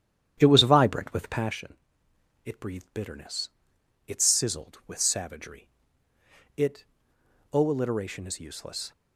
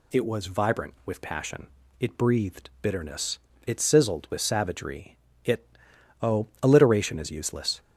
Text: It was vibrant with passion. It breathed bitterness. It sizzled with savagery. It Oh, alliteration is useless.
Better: second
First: starts louder than the rest; strong; until 1.6 s; 10 dB // pauses between "It" and "Oh"; noticeable; at 6.8 s; 0.68 s long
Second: pauses between "It" and "Oh"; noticeable; at 5.6 s; 0.56 s long

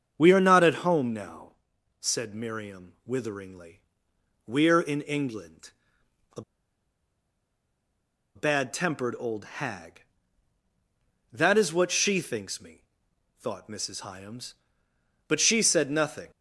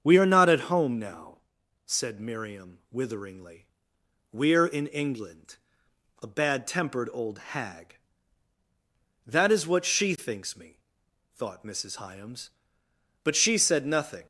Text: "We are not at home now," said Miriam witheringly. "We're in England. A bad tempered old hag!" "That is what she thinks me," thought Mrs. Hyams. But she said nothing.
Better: second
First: starts louder than the rest; strong; until 1.1 s; 7 dB // pauses between "A" and "bad"; strong; at 6.4 s; 1.9 s long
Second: starts louder than the rest; strong; until 1.0 s; 7 dB

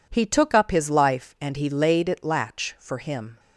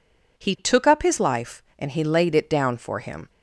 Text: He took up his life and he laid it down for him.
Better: second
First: says "latch" for "down"; at 2.2 s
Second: none

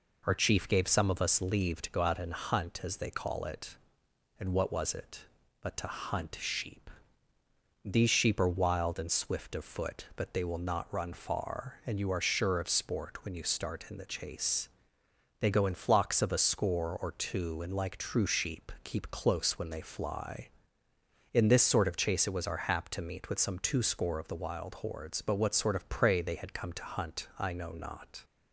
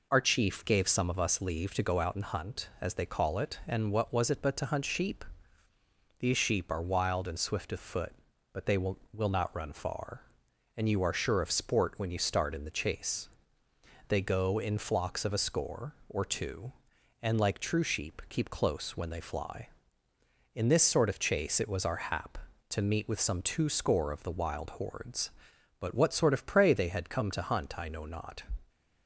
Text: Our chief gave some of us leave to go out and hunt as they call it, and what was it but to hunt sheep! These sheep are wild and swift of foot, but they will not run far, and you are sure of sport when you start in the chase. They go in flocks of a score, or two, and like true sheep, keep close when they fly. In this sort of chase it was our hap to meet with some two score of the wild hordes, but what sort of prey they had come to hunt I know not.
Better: first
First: none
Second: says "will" twice; at 9.1 s

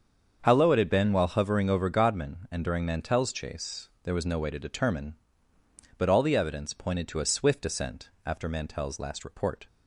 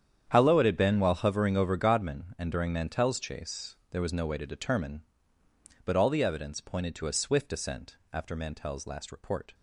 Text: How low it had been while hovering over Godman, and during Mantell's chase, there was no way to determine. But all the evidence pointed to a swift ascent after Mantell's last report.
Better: first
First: starts louder than the rest; until 1.4 s; 7 dB // pauses between "ascent" and "after"; slight; at 8.0 s; 0.16 s long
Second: gets quieter; strong; throughout; 15 dB // starts louder than the rest; strong; until 1.3 s; 9 dB // pauses between "ascent" and "after"; slight; at 7.9 s; 0.16 s long

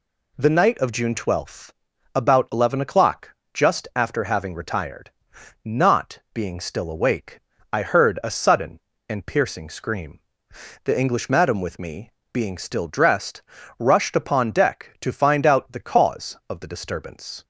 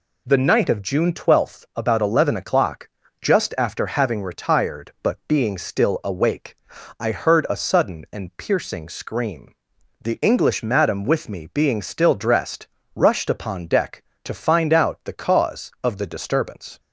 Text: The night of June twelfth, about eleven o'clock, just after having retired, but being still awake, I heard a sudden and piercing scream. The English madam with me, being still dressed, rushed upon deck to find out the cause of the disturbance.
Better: second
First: says "not" for "but"; at 5.6 s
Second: none

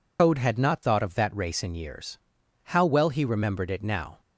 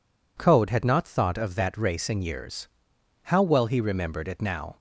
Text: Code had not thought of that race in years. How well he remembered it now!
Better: second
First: loses the start of "Code"; at 0.1 s; 100 ms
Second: none

